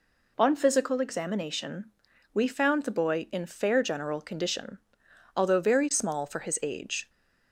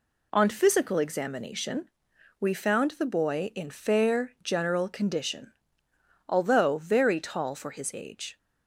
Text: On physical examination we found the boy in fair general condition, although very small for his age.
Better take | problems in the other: first | pauses between "examination" and "we"; noticeable; at 1.8 s; 0.52 s long; noticeable in the first // says "tall" for "small"; at 7.1 s

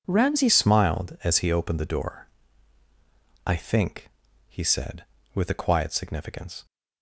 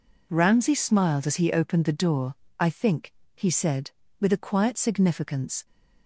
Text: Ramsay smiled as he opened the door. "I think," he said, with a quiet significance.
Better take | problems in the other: second | changes voice at "smiled"; from 0.4 s on; 6.2 s long

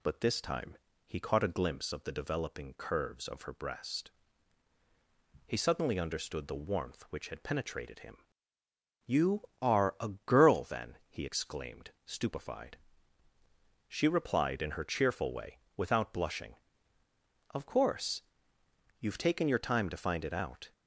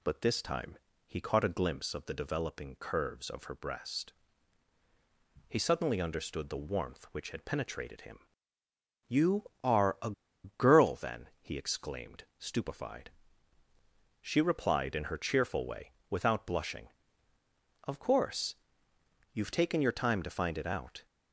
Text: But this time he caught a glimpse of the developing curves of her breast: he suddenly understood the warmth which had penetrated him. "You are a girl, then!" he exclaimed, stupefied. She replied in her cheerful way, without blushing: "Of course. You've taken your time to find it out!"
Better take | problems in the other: first | pauses between "time" and "he"; slight; at 0.7 s; 0.30 s long; slight in the first // pauses between "a" and "girl"; slight; at 10.1 s; 0.32 s long

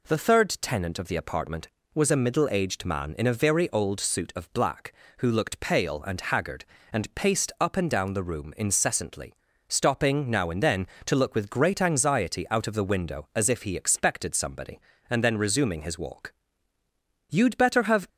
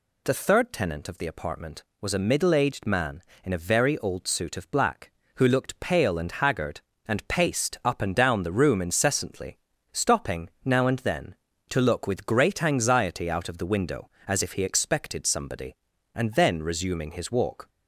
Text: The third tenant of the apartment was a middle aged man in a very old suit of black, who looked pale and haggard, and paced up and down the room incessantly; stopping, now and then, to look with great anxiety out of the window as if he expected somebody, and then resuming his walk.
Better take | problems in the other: second | goes on to say "You'd better have"; noticeable; from 17.2 s on; 0.78 s long

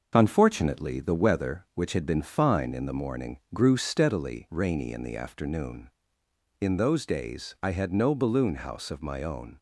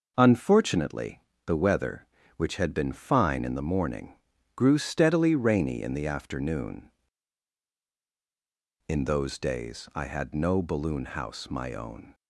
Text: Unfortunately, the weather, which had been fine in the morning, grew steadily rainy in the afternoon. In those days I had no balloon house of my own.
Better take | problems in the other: first | skips "of"; at 11.4 s

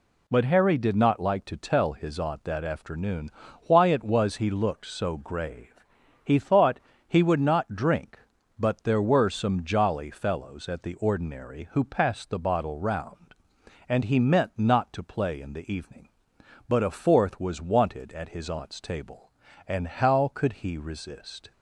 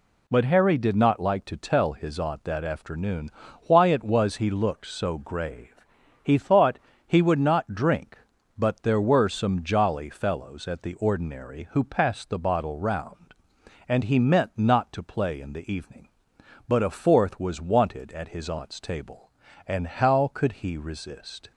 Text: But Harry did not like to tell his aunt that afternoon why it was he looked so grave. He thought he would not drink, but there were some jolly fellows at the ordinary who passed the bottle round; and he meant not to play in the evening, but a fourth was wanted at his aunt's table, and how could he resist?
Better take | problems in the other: neither | pauses between "afternoon" and "why"; slight; the same in both // pauses between "thought" and "he"; slight; the same in both

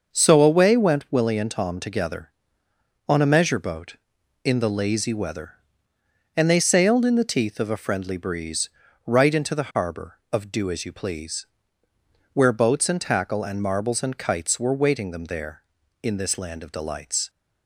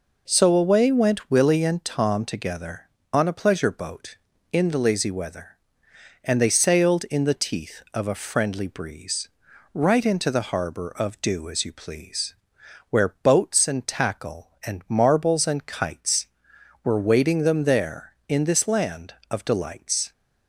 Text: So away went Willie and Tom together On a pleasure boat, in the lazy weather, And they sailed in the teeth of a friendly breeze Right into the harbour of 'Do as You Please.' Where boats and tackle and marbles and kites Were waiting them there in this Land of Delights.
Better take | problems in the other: second | starts louder than the rest; noticeable; until 1.1 s; 6 dB // says "measure" for "pleasure"; at 3.3 s // pauses between "breeze" and "Right"; at 8.6 s; 0.38 s long; also in the second

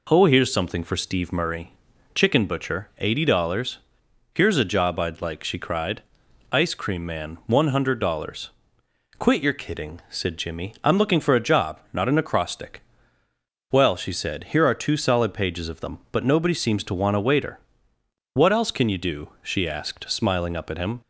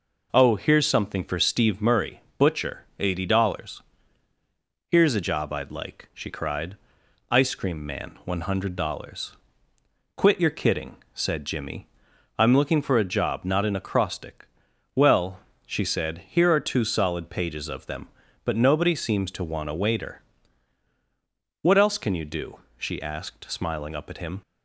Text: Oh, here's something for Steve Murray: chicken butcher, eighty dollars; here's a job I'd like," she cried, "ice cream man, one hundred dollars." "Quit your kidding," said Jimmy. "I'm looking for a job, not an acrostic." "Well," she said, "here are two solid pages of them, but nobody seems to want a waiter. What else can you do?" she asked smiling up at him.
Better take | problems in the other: first | skips "chicken"; at 2.2 s

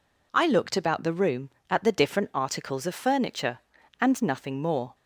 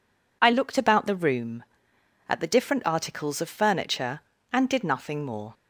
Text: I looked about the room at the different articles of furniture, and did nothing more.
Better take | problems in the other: second | skips "did"; at 4.2 s

